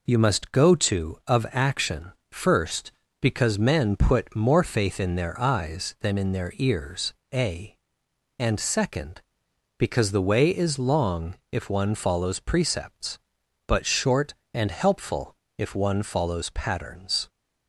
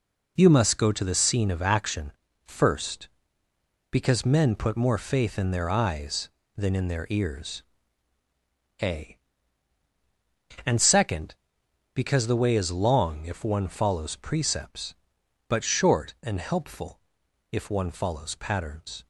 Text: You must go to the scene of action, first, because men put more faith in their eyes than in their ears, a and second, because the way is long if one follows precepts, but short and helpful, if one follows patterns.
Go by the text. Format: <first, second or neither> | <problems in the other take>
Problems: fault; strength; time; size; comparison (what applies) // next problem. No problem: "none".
second | skips "the scene"; at 1.2 s // pauses between "long" and "if"; slight; at 11.3 s; 0.16 s long